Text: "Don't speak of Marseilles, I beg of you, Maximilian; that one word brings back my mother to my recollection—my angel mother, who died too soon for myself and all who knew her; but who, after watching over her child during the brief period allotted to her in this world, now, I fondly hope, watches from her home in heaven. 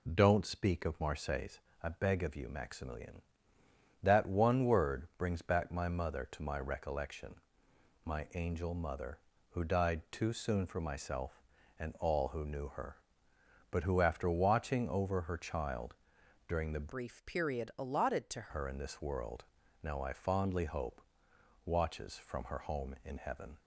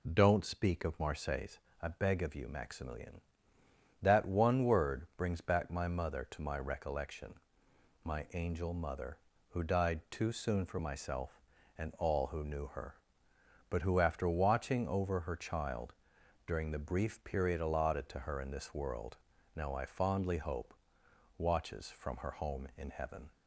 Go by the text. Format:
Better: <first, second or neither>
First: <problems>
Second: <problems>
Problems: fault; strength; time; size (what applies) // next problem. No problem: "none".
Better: second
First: pauses between "child" and "during"; noticeable; at 15.9 s; 0.50 s long // changes voice from "brief" to "to"; from 16.9 to 18.4 s; 1.5 s long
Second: pauses between "child" and "during"; noticeable; at 15.9 s; 0.50 s long